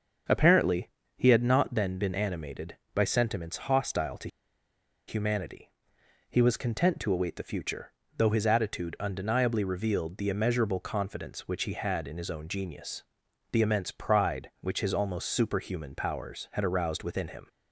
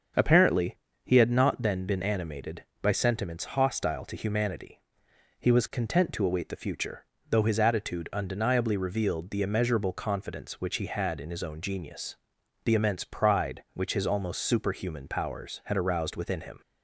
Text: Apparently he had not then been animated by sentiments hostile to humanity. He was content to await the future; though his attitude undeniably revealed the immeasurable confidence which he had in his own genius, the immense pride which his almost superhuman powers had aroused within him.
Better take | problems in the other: second | starts louder than the rest; until 1.5 s; 6.5 dB; also in the second // pauses between "Apparently" and "he"; slight; at 0.8 s; 0.28 s long; slight in the second // pauses between "to" and "humanity"; noticeable; at 4.2 s; 0.79 s long

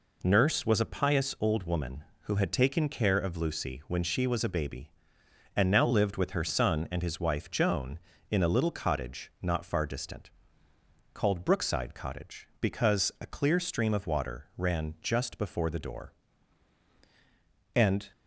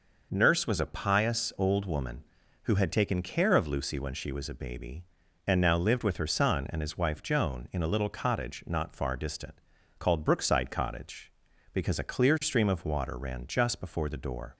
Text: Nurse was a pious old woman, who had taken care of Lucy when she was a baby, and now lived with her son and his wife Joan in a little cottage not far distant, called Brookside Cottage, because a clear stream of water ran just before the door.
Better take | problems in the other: second | goes on to say "And"; slight; from 17.7 s on; 0.36 s long

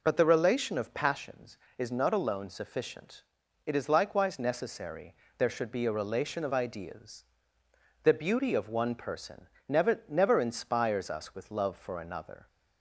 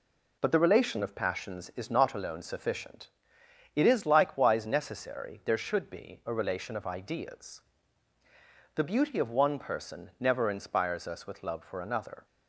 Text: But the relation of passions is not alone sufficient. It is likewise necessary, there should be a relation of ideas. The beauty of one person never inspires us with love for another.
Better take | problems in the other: second | pauses between "person" and "never"; slight; at 9.4 s; 0.22 s long // says "never" twice; at 10.0 s

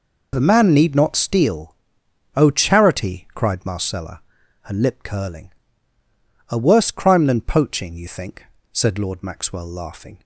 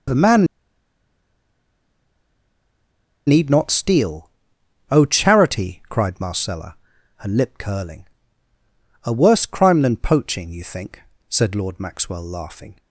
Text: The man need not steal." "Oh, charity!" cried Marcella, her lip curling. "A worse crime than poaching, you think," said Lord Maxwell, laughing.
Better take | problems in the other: first | pauses between "man" and "need"; strong; at 0.4 s; 2.8 s long

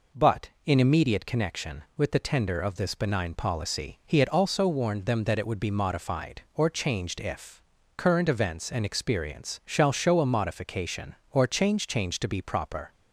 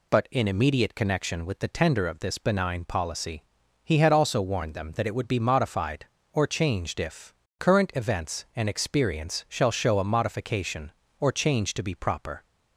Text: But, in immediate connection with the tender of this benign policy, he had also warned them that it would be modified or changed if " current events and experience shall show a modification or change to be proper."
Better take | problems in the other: second | says "change" twice; at 11.8 s

